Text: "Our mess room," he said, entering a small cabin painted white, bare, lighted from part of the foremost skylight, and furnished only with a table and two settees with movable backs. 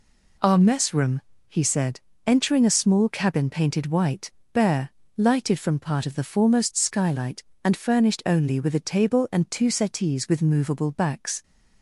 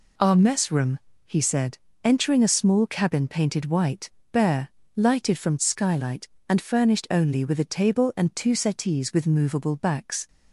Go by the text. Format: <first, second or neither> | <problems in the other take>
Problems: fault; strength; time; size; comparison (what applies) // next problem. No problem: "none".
first | skips "part of the foremost"; at 5.5 s